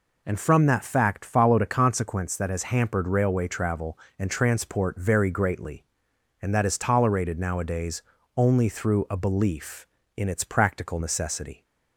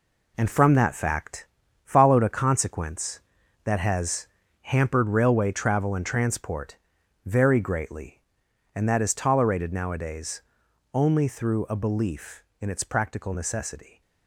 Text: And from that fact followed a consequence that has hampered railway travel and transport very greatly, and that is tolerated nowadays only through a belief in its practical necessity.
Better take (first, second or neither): first